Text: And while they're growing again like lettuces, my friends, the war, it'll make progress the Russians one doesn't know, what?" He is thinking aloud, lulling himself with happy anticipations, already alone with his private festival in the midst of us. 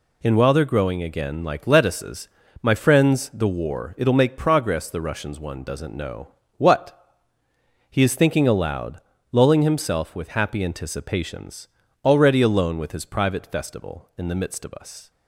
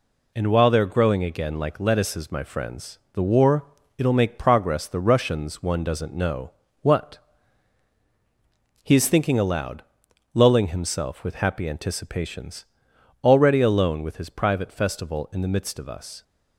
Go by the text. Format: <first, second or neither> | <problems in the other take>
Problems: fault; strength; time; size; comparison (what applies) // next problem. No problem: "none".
neither | none